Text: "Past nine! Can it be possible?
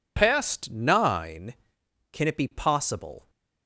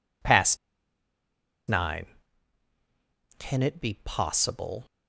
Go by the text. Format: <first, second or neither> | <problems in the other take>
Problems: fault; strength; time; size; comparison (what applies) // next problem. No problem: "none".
first | pauses between "Past" and "nine"; at 0.5 s; 1.1 s long